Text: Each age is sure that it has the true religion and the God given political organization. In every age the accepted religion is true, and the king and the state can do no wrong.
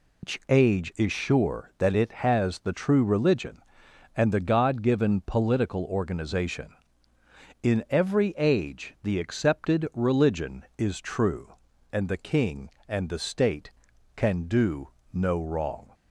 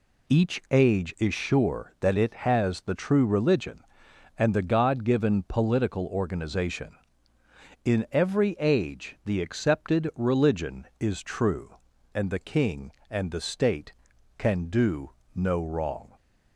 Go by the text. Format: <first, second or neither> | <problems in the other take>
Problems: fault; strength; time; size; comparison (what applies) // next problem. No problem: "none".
second | loses the start of "Each"; at 0.2 s; 165 ms // pauses between "do" and "no"; slight; at 14.8 s; 0.24 s long; slight in the second